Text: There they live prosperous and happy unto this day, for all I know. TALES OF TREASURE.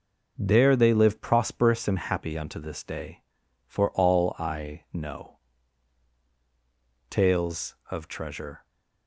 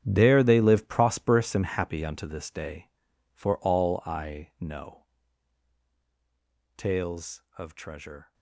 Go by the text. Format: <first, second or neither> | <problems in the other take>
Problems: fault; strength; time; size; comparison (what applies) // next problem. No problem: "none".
first | gets quieter; strong; throughout; 15 dB